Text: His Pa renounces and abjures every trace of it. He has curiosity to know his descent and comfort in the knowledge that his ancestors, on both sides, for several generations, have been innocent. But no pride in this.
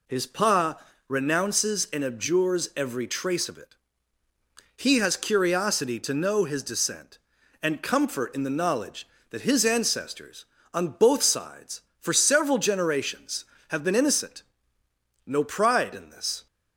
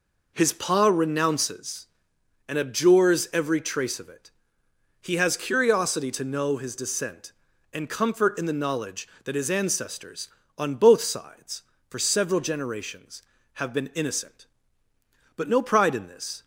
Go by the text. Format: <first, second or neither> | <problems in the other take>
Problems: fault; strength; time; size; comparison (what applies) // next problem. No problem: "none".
second | pauses between "Pa" and "renounces"; slight; at 0.7 s; 0.32 s long // skips "But"; at 14.8 s